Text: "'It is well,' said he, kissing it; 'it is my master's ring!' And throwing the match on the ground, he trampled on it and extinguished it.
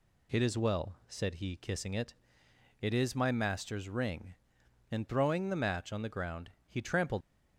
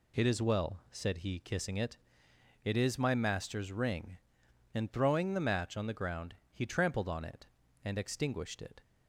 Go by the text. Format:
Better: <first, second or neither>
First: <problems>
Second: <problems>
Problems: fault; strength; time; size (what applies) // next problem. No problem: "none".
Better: second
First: stops before "on it and extinguished it"; at 7.2 s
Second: none